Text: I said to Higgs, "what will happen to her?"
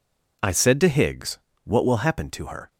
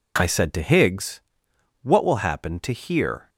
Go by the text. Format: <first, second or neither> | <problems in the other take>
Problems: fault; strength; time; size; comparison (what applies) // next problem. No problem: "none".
first | says "here" for "her"; at 2.7 s